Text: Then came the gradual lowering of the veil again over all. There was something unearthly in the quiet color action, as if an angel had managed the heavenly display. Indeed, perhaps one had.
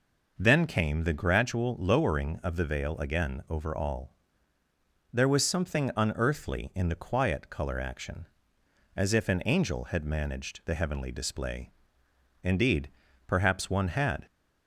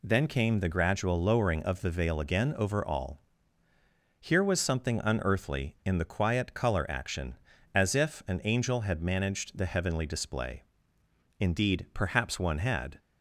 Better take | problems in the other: first | says "Here" for "There"; at 4.1 s

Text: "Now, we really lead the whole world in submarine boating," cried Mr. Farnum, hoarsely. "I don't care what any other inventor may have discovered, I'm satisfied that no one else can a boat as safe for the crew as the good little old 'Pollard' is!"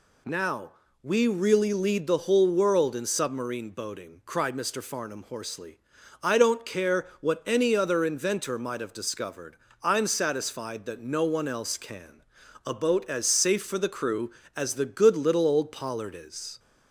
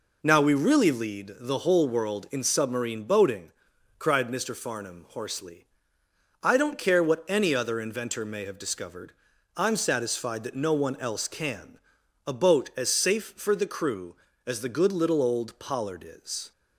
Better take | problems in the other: second | says "might" for "may"; at 8.5 s // pauses between "can" and "a"; at 12.2 s; 0.42 s long; noticeable in the second

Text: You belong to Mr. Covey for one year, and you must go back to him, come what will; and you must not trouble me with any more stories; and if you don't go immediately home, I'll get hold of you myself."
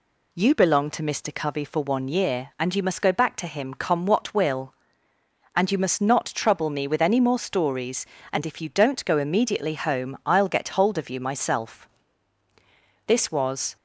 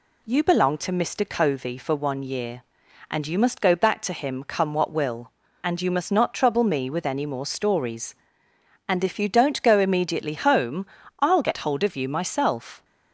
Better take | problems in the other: second | goes on to say "This was"; noticeable; from 13.0 s on; 0.68 s long

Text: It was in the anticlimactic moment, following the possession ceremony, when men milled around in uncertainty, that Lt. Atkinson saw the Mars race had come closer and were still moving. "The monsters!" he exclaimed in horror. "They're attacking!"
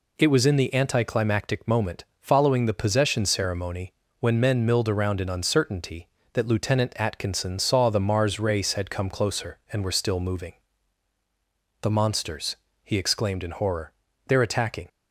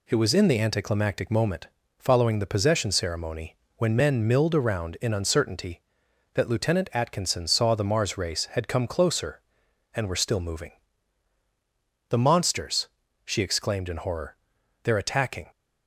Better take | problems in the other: first | says "she" for "he"; at 13.2 s

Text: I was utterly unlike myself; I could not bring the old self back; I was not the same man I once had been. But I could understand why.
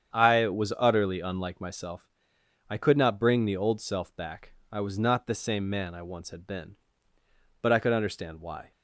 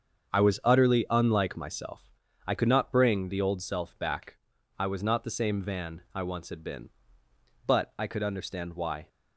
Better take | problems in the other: first | starts louder than the rest; strong; until 1.3 s; 7 dB; strong in the first // says "van" for "man"; at 5.6 s

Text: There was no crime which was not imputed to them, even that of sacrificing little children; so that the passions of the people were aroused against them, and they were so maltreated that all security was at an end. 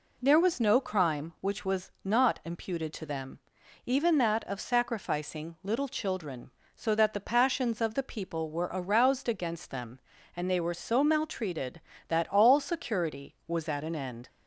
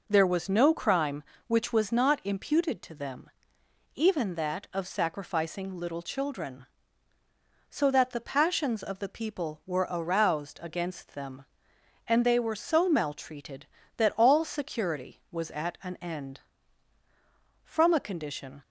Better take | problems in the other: first | goes on to say "From a condition"; noticeable; from 17.6 s on; 0.98 s long

